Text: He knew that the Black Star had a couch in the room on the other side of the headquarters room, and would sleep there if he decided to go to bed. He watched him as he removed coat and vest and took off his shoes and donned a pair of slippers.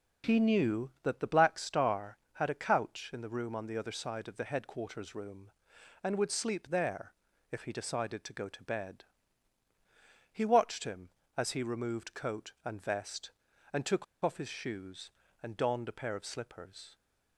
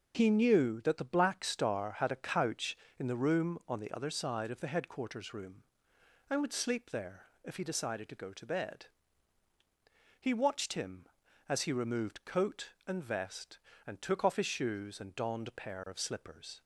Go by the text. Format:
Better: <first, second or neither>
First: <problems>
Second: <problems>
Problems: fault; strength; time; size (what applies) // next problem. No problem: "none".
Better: second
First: pauses between "there" and "if"; at 7.1 s; 0.38 s long // pauses between "took" and "off"; slight; at 14.0 s; 0.19 s long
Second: pauses between "there" and "if"; slight; at 7.2 s; 0.18 s long